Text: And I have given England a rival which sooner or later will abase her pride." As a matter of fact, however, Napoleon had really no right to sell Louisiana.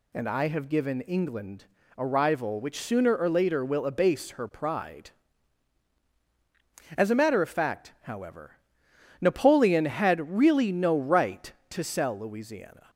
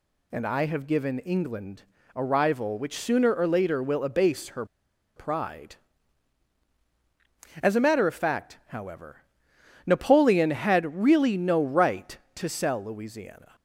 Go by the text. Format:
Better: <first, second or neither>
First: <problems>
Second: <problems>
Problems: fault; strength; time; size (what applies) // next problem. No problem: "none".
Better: first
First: pauses between "England" and "a"; slight; at 1.6 s; 0.32 s long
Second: pauses between "England" and "a"; slight; at 1.8 s; 0.32 s long // pauses between "her" and "pride"; noticeable; at 4.6 s; 0.51 s long